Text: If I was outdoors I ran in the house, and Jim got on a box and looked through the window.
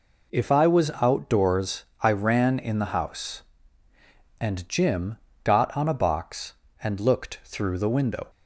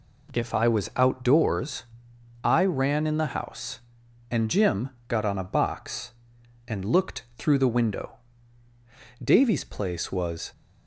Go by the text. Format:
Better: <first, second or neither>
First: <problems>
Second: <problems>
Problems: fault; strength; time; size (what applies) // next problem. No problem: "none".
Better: first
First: pauses between "outdoors" and "I"; slight; at 1.8 s; 0.18 s long // pauses between "Jim" and "got"; slight; at 5.1 s; 0.24 s long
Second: pauses between "outdoors" and "I"; noticeable; at 1.8 s; 0.58 s long // pauses between "Jim" and "got"; slight; at 4.8 s; 0.18 s long // goes on to say "Davy's place was"; noticeable; from 9.2 s on; 1.2 s long